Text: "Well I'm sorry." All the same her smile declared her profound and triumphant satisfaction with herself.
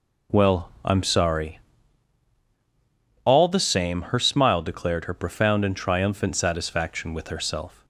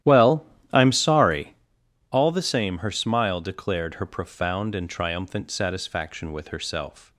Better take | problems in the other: first | starts louder than the rest; strong; until 1.6 s; 12.5 dB // pauses between "Well" and "I'm"; slight; at 0.4 s; 0.30 s long

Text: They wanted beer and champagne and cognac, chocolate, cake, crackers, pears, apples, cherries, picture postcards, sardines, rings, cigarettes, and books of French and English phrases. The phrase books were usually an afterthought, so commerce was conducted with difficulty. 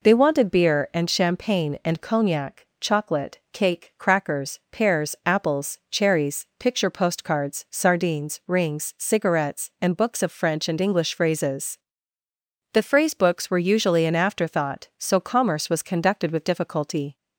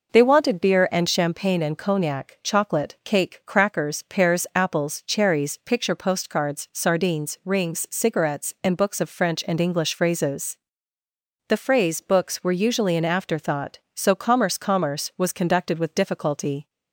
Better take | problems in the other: first | says "commerce" twice; at 14.5 s

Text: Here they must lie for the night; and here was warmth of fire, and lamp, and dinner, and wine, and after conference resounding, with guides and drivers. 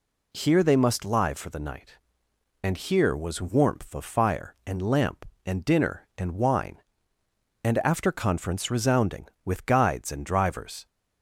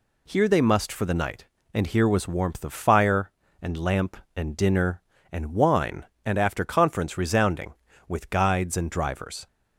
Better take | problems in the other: first | skips "lie"; at 0.9 s

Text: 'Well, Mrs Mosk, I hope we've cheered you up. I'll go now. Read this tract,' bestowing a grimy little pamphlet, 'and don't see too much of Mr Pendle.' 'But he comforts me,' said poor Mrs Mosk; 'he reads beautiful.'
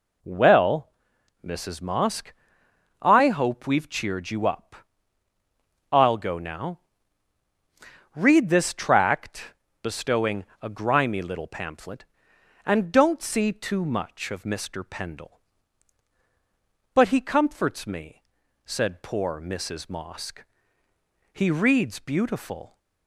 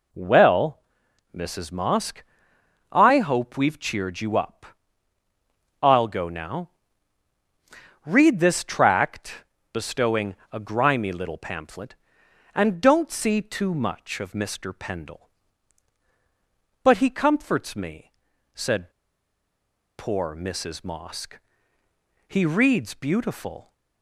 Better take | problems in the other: first | pauses between "bestowing" and "a"; slight; at 10.3 s; 0.16 s long; slight in the first // pauses between "said" and "poor"; at 18.9 s; 1.0 s long

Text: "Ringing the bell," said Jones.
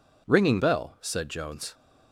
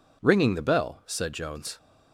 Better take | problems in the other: second | skips "the"; at 0.5 s

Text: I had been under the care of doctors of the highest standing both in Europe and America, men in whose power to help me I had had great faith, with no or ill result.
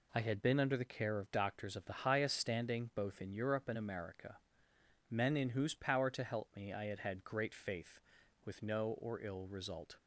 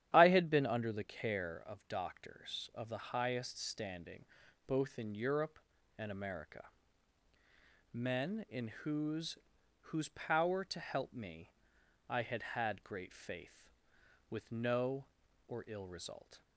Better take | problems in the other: first | starts louder than the rest; strong; until 1.1 s; 10.5 dB // pauses between "standing" and "both"; at 4.2 s; 0.42 s long // says "whose" twice; at 9.8 s // pauses between "me" and "I"; noticeable; at 11.5 s; 0.58 s long

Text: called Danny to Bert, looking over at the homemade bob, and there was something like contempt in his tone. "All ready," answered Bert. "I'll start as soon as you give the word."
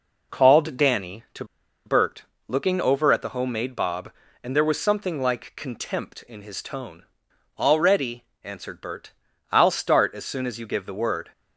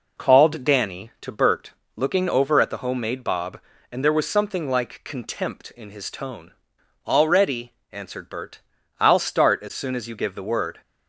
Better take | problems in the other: second | pauses between "to" and "Bert"; at 1.4 s; 0.41 s long

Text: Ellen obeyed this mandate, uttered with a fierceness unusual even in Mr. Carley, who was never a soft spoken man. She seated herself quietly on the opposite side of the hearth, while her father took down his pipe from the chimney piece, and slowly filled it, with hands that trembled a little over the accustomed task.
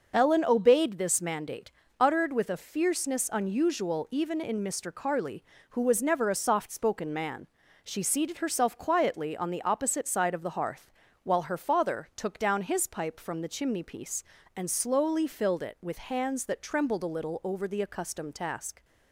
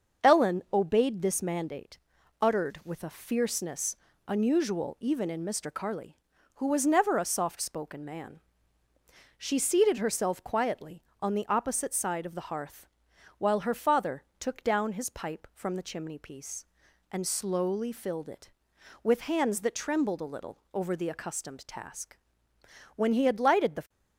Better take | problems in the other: first | starts louder than the rest; until 1.3 s; 6.5 dB // pauses between "fierceness" and "unusual"; slight; at 3.9 s; 0.32 s long // pauses between "father" and "took"; slight; at 14.2 s; 0.18 s long // goes on to say "When he had lighted the"; noticeable; from 22.9 s on; 0.92 s long

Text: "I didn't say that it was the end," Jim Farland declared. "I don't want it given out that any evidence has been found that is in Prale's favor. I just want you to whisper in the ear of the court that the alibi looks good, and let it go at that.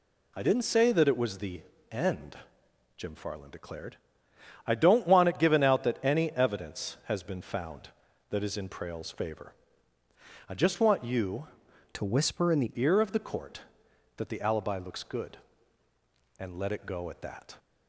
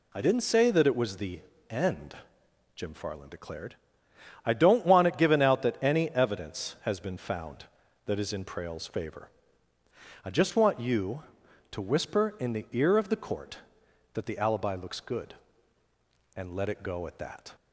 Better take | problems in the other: second | pauses between "the" and "end"; slight; at 1.6 s; 0.30 s long; slight in the second // changes voice from "to" to "the"; from 11.9 to 12.7 s; 0.8 s long

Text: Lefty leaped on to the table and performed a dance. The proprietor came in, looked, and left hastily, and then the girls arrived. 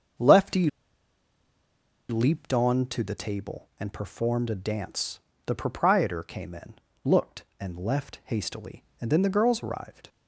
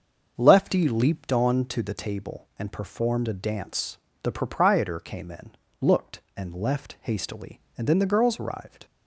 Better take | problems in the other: second | starts louder than the rest; until 2.6 s; 6.5 dB; also in the second // pauses between "Lefty" and "leaped"; strong; at 0.6 s; 1.4 s long

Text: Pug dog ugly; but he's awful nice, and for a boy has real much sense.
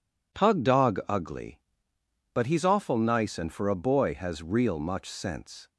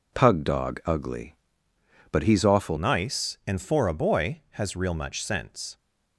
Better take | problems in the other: first | changes voice at "nice"; from 2.7 s on; 3.0 s long

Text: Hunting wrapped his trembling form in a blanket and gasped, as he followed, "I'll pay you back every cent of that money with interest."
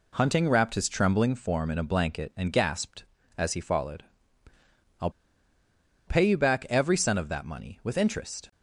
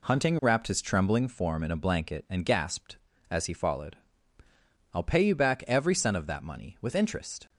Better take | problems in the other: second | pauses between "I'll" and "pay"; noticeable; at 5.0 s; 0.97 s long

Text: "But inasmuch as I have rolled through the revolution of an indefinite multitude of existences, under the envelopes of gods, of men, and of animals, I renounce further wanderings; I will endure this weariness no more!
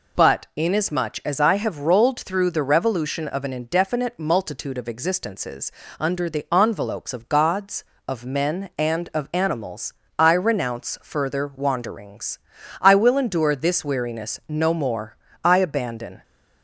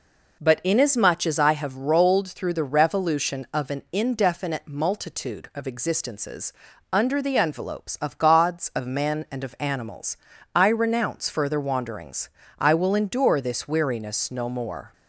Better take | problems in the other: second | goes on to say "I abandon"; noticeable; from 15.4 s on; 0.78 s long

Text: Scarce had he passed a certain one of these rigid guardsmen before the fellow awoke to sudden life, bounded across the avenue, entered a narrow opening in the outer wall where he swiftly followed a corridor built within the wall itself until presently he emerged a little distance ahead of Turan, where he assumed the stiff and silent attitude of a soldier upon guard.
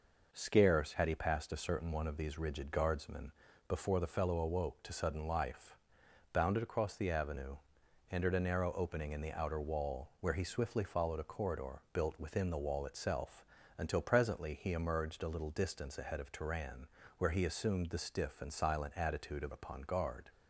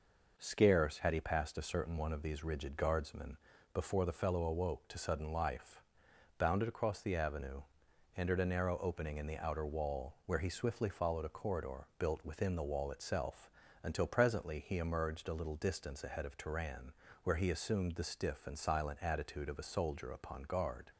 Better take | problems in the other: second | pauses between "guardsmen" and "before"; slight; at 3.3 s; 0.36 s long; slight in the second // pauses between "itself" and "until"; slight; at 13.4 s; 0.34 s long; slight in the second // skips "a soldier"; at 19.5 s

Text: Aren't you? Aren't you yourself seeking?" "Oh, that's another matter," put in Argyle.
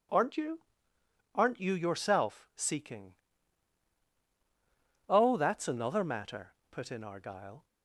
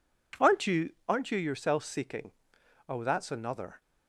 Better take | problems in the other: first | stops before "matter put in Argyle"; at 3.8 s

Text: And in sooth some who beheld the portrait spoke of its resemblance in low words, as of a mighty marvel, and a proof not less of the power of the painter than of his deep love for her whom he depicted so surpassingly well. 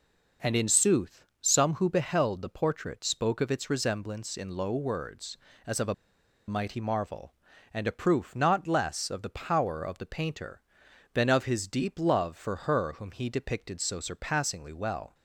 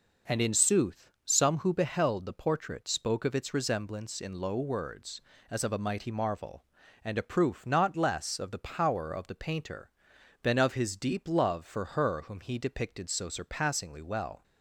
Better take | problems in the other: second | pauses between "sooth" and "some"; slight; at 1.2 s; 0.18 s long; slight in the second // pauses between "a" and "mighty"; noticeable; at 5.9 s; 0.53 s long

